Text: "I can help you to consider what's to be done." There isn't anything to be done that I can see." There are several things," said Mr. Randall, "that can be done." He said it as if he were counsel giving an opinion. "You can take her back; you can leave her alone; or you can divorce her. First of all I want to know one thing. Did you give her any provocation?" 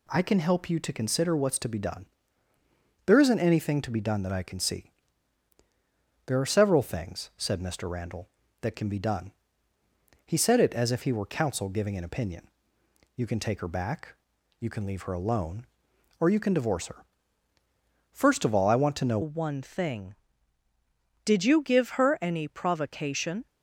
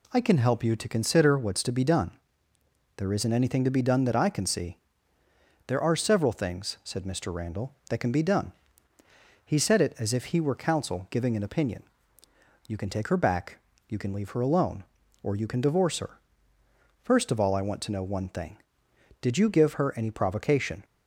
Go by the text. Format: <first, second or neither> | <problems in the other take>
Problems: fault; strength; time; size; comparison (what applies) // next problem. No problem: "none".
second | changes voice at "one"; from 19.2 s on; 4.2 s long